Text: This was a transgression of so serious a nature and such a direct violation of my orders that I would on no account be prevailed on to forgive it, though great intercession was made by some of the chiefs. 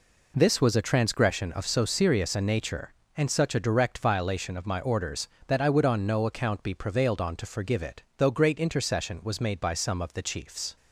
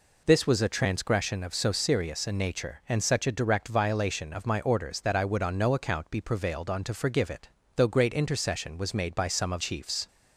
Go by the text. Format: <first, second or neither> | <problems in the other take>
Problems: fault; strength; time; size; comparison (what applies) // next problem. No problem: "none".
first | skips "the"; at 9.6 s